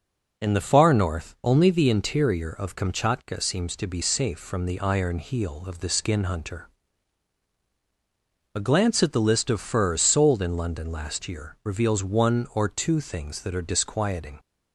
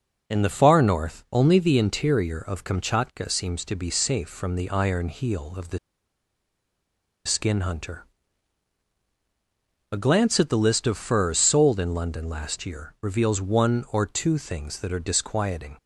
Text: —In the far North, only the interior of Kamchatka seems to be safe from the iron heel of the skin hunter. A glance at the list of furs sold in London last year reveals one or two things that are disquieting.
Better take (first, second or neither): first